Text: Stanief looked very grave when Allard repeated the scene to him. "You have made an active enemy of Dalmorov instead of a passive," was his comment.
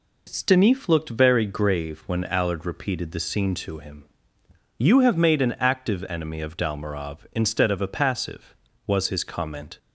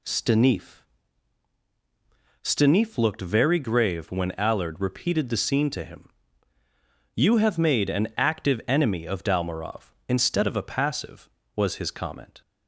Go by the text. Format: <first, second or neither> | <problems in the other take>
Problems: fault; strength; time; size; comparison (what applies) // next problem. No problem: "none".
first | says "Stanief" twice; at 2.4 s